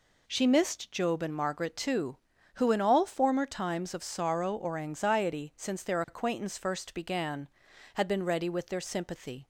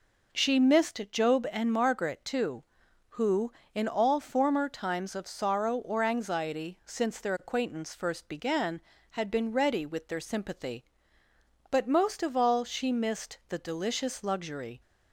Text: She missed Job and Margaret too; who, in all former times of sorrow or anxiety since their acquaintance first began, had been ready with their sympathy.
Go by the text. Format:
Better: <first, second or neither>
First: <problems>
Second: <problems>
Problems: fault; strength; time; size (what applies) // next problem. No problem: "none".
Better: first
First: none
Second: goes on to say "But most of all she missed the delicious luxury"; strong; from 11.7 s on; 3.1 s long